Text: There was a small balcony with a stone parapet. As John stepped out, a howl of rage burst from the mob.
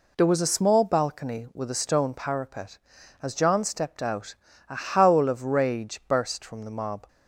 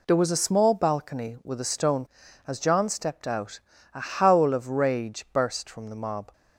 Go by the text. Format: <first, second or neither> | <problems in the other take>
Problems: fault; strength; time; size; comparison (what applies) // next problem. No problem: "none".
first | skips "parapet"; at 2.2 s